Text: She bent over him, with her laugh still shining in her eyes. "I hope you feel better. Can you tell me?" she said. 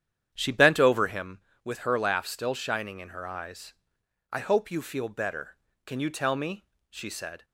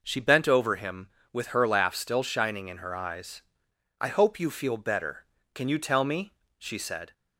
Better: second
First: starts louder than the rest; strong; until 1.3 s; 9.5 dB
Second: none

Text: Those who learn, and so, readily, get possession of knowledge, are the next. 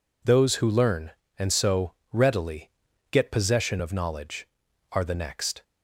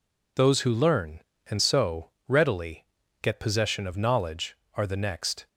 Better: neither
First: none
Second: none

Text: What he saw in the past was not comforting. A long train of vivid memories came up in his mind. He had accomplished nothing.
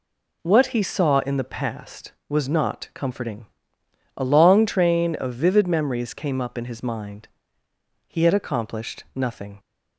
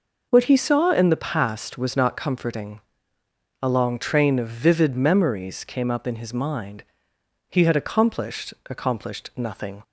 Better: first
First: none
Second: says "accomplished" twice; at 8.6 s

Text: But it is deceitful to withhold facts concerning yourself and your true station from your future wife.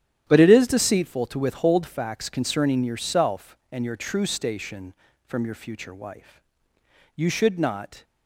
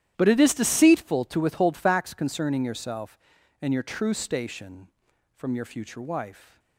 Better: second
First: starts louder than the rest; strong; until 1.3 s; 10.5 dB // goes on to say "You should not"; noticeable; from 7.1 s on; 0.88 s long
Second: starts louder than the rest; strong; until 1.1 s; 11.5 dB

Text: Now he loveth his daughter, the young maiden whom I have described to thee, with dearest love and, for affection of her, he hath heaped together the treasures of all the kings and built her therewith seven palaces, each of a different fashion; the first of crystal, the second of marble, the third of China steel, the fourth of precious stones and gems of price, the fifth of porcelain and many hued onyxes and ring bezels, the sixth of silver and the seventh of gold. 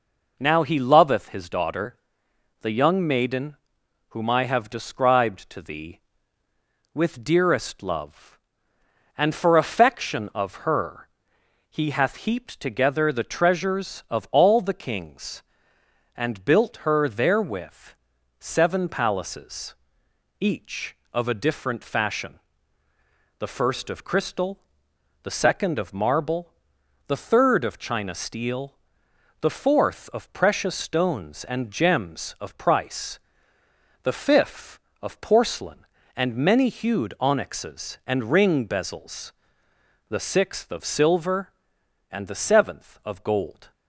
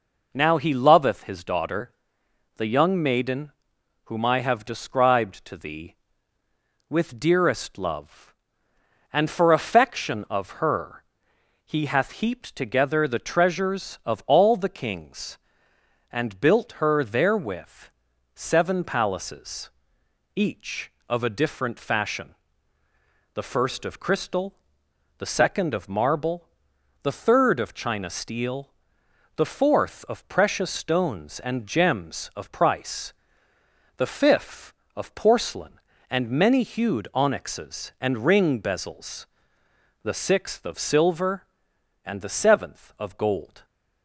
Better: neither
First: pauses between "maiden" and "whom"; noticeable; at 3.5 s; 0.52 s long // pauses between "therewith" and "seven"; at 17.9 s; 0.44 s long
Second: pauses between "maiden" and "whom"; noticeable; at 3.5 s; 0.52 s long // pauses between "therewith" and "seven"; at 17.8 s; 0.44 s long

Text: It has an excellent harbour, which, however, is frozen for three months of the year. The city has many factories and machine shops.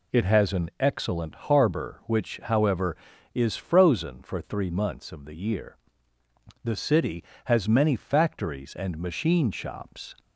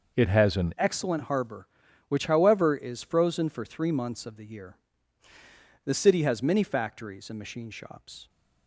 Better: first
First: none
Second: changes voice at "excellent"; from 0.7 s on; 7.5 s long

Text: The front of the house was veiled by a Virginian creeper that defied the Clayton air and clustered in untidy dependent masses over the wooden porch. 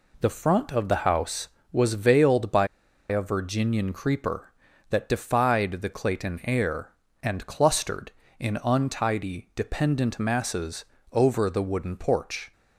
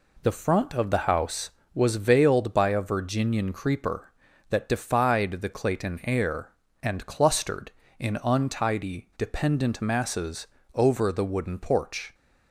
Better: second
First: pauses between "by" and "a"; at 2.6 s; 0.42 s long // pauses between "masses" and "over"; slight; at 10.8 s; 0.28 s long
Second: pauses between "masses" and "over"; slight; at 10.4 s; 0.28 s long

